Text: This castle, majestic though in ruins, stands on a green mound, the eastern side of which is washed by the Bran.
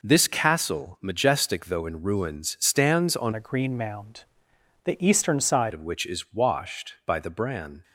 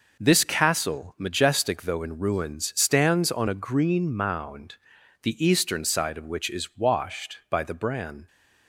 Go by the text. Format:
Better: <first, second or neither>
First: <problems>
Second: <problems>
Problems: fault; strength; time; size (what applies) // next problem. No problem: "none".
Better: second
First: changes voice from "a" to "side"; from 3.3 to 5.7 s; 2.4 s long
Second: none